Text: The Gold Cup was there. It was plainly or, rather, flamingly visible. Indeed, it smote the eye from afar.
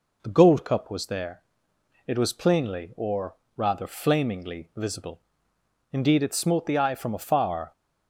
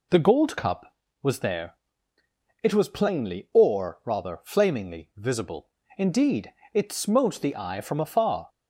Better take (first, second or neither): neither